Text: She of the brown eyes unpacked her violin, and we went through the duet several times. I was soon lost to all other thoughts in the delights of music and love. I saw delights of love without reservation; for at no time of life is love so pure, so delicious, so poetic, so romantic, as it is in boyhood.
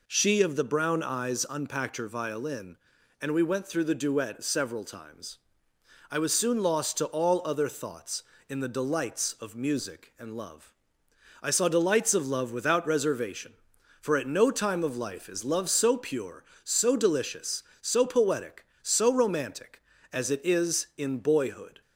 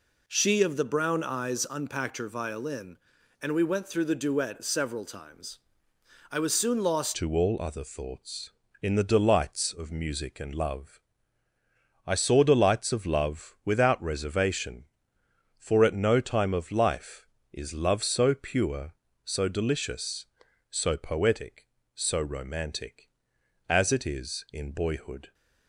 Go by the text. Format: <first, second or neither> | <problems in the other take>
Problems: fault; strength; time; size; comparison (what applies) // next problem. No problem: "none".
first | changes voice at "to"; from 7.1 s on; 18.2 s long